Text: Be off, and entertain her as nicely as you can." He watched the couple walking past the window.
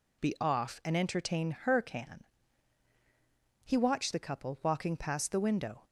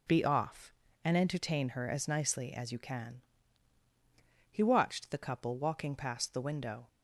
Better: second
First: skips "as nicely as you"; at 1.8 s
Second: none

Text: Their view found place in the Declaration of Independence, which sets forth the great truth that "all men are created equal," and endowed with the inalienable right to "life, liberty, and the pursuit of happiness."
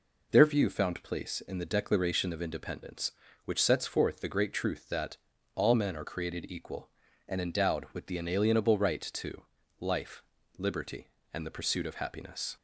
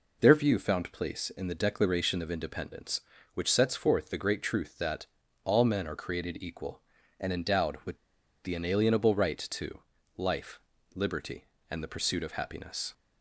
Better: first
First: pauses between "that" and "all"; at 5.1 s; 0.38 s long // pauses between "to" and "life"; slight; at 9.4 s; 0.32 s long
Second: pauses between "that" and "all"; at 5.0 s; 0.38 s long // pauses between "with" and "the"; noticeable; at 7.9 s; 0.47 s long // pauses between "to" and "life"; slight; at 9.8 s; 0.32 s long

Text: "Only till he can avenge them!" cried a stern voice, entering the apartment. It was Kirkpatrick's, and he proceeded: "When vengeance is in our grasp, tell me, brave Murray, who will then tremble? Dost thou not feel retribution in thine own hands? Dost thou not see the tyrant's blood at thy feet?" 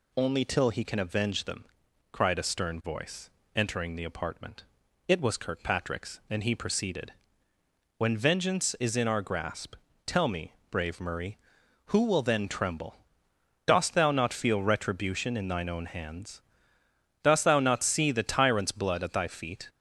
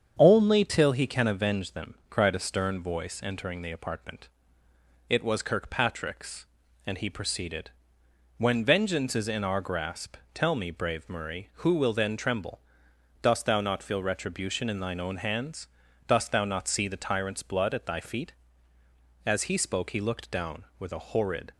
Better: first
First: none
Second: starts louder than the rest; strong; until 1.2 s; 7.5 dB // goes on to say "As he spoke he looked down with a horrid"; strong; from 19.2 s on; 2.2 s long

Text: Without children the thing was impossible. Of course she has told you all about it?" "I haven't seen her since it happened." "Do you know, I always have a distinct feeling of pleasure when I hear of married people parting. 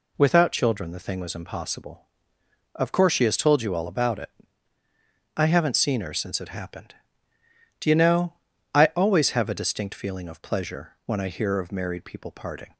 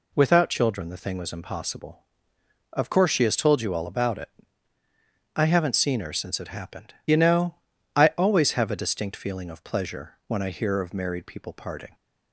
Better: first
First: none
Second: skips "Do"; at 7.0 s

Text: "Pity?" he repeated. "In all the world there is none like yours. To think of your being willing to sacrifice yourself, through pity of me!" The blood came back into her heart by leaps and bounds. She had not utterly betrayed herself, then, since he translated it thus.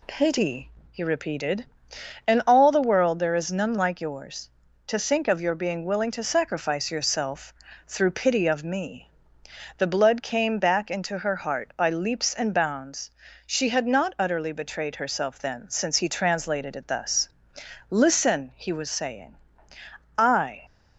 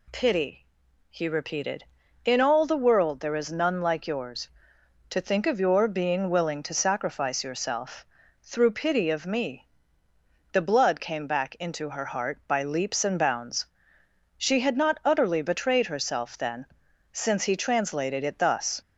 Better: second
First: goes on to say "Listen he was saying I"; strong; from 17.8 s on; 2.7 s long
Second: none

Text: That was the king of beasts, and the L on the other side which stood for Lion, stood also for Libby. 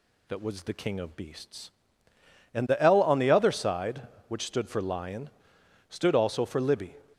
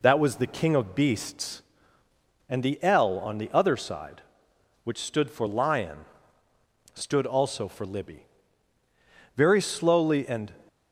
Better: first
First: none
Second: goes on to say "Very slowly and"; noticeable; from 9.3 s on; 1.1 s long

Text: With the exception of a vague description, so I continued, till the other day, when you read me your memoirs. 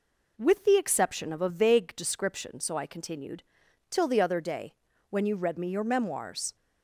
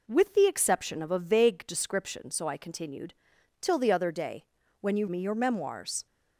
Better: first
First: none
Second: skips "read"; at 5.0 s

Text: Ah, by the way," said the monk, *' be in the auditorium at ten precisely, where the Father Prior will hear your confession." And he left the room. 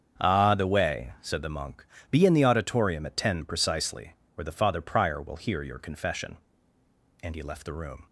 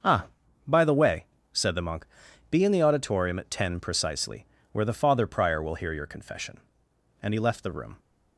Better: second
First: starts louder than the rest; strong; until 1.2 s; 7 dB // skips "by"; at 0.5 s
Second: starts louder than the rest; until 1.6 s; 6.5 dB

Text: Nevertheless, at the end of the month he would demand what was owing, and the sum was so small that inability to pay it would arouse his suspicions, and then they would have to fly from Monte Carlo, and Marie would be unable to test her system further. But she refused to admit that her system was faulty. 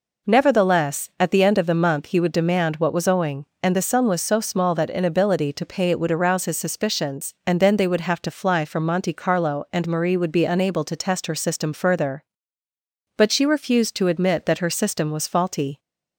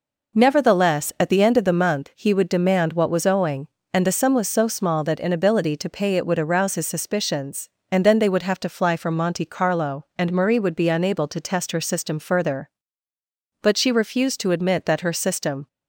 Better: first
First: none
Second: stops before "was faulty"; at 15.6 s

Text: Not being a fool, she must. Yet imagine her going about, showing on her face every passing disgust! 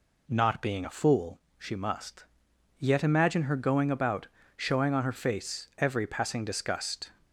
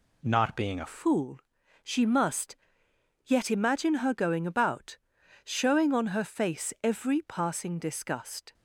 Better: first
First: none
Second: changes voice at "fool"; from 0.8 s on; 7.7 s long

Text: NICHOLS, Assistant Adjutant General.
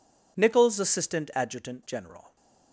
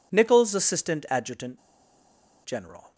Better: first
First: none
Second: pauses between "Adjutant" and "General"; noticeable; at 1.5 s; 0.85 s long

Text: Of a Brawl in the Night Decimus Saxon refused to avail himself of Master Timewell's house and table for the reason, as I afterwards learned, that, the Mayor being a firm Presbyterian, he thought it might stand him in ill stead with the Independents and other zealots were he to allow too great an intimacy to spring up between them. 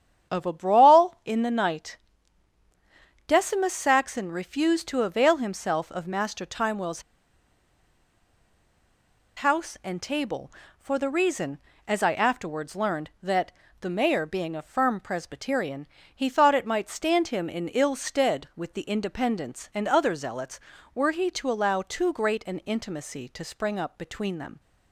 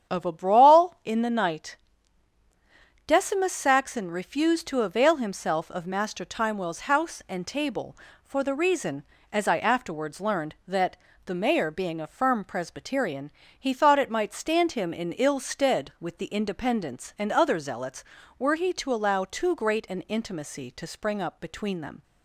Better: second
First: starts louder than the rest; strong; until 1.3 s; 9 dB // pauses between "Night" and "Decimus"; strong; at 1.9 s; 1.3 s long // pauses between "Timewell's" and "house"; strong; at 7.0 s; 2.3 s long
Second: starts louder than the rest; strong; until 1.1 s; 9 dB // pauses between "Night" and "Decimus"; strong; at 1.7 s; 1.3 s long

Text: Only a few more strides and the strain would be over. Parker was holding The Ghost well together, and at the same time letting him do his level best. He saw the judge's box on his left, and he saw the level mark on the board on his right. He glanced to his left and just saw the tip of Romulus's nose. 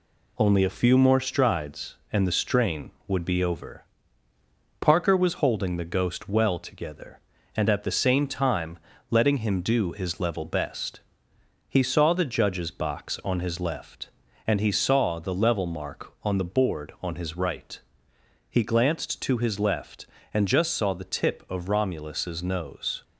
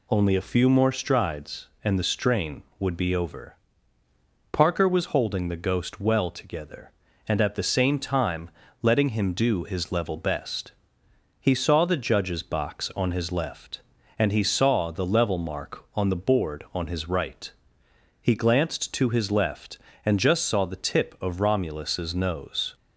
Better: second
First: gets quieter; throughout; 4 dB // pauses between "time" and "letting"; slight; at 8.7 s; 0.32 s long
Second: pauses between "time" and "letting"; slight; at 8.4 s; 0.32 s long

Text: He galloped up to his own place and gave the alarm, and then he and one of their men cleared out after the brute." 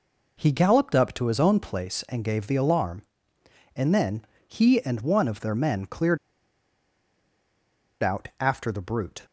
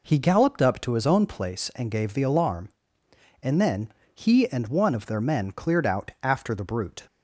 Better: second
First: pauses between "then" and "he"; slight; at 4.2 s; 0.22 s long // pauses between "cleared" and "out"; strong; at 6.1 s; 1.8 s long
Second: pauses between "then" and "he"; slight; at 3.9 s; 0.22 s long

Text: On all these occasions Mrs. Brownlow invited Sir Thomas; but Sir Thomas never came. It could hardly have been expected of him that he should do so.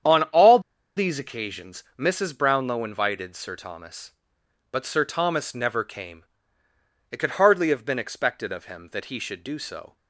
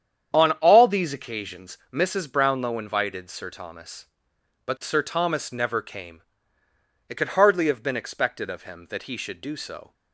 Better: second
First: starts louder than the rest; strong; until 1.4 s; 9 dB // pauses between "all" and "these"; at 0.5 s; 0.37 s long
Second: starts louder than the rest; strong; until 1.3 s; 9 dB

